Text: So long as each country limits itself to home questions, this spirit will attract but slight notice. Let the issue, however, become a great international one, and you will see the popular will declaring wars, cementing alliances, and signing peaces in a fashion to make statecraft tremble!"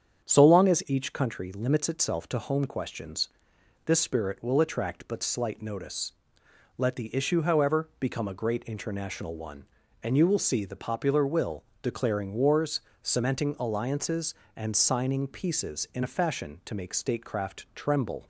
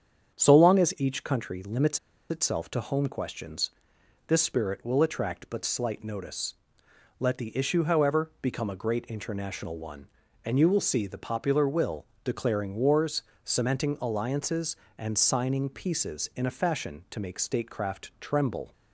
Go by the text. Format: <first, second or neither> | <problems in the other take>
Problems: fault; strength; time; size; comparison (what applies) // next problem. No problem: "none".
first | starts louder than the rest; strong; until 1.3 s; 8 dB; strong in the first // pauses between "limits" and "itself"; slight; at 1.9 s; 0.31 s long // pauses between "will" and "declaring"; slight; at 12.0 s; 0.18 s long; slight in the first